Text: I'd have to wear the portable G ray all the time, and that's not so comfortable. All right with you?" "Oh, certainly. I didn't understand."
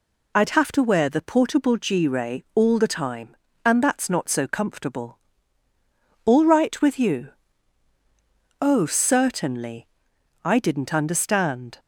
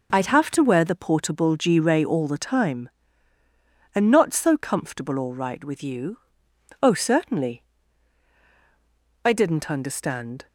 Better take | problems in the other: first | skips "that's"; at 4.1 s

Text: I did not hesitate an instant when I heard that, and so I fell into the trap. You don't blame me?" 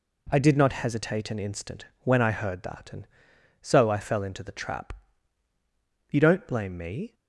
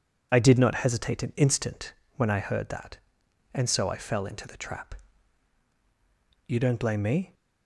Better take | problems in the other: neither | pauses between "instant" and "when"; slight; the same in both

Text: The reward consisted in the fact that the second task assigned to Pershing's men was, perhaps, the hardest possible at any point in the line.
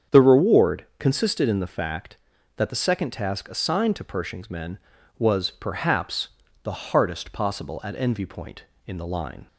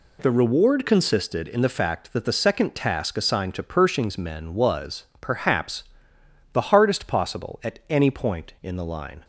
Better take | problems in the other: second | starts louder than the rest; strong; until 1.2 s; 7.5 dB // says "envy" for "any"; at 7.9 s

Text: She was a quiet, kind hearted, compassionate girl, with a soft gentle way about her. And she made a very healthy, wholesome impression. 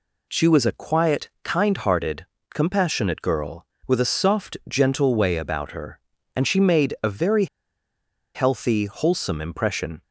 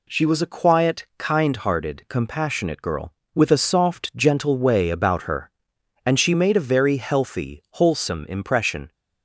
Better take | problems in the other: second | pauses between "very" and "healthy"; noticeable; at 7.4 s; 0.89 s long

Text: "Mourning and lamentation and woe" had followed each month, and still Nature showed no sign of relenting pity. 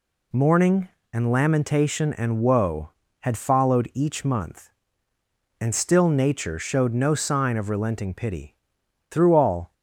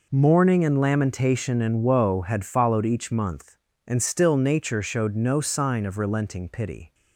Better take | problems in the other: second | goes on to say "Through all"; noticeable; from 9.0 s on; 0.64 s long

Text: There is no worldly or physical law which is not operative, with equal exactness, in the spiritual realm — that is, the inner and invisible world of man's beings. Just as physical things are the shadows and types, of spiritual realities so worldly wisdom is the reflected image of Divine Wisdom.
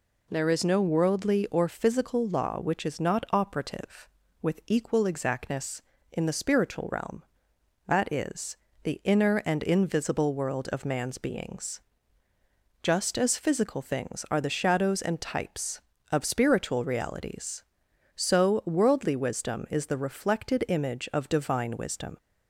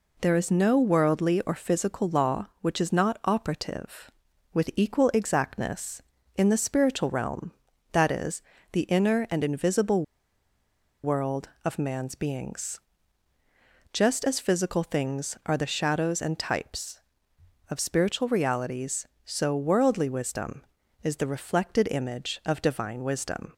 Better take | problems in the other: first | pauses between "invisible" and "world"; at 10.0 s; 0.99 s long

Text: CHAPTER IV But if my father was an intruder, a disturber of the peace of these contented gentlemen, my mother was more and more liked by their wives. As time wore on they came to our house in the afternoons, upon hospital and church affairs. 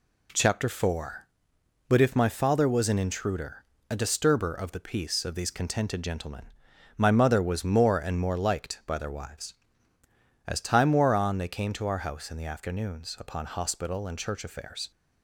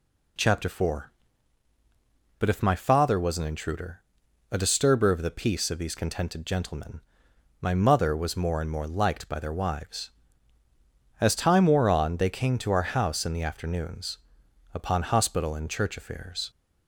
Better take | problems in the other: neither | none

